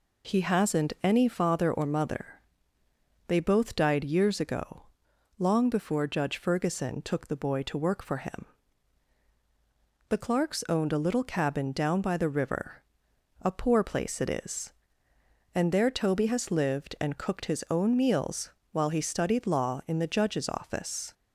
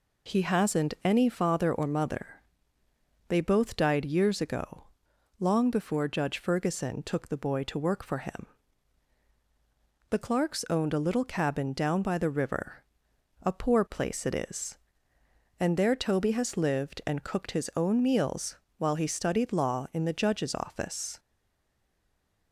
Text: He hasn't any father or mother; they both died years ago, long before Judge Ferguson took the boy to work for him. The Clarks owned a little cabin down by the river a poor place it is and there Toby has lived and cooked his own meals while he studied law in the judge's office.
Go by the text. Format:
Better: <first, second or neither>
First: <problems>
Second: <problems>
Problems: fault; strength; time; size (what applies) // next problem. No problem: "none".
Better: first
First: pauses between "river" and "a"; noticeable; at 12.8 s; 0.60 s long // pauses between "meals" and "while"; slight; at 18.4 s; 0.22 s long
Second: pauses between "river" and "a"; noticeable; at 12.8 s; 0.60 s long // pauses between "meals" and "while"; slight; at 18.5 s; 0.22 s long // stays silent after the last word; noticeable; from 21.1 s on; 1.4 s long